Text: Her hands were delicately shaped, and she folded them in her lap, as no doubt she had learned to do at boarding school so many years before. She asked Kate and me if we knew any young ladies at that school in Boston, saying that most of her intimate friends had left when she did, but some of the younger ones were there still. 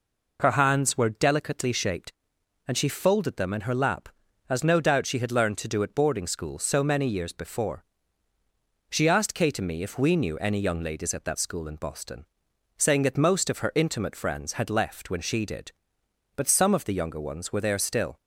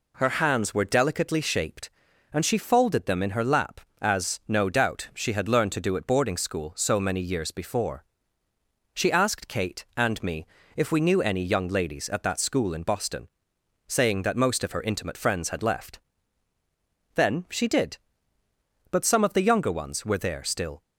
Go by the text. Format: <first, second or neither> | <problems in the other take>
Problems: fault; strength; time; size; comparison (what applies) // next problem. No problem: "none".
first | pauses between "me" and "if"; slight; at 10.4 s; 0.30 s long // says "then" for "when"; at 17.1 s